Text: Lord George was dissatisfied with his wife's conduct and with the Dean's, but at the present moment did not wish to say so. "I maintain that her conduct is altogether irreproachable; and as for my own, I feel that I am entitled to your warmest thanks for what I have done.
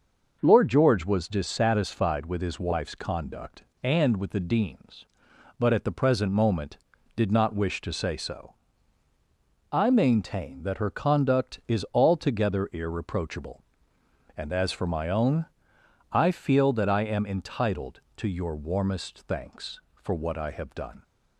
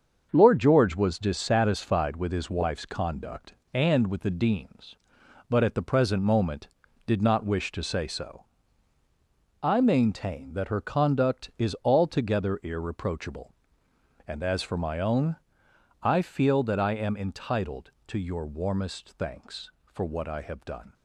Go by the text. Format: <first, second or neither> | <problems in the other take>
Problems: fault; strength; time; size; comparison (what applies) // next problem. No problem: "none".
first | gets quieter; strong; throughout; 7 dB // starts louder than the rest; until 1.3 s; 7 dB; noticeable in the first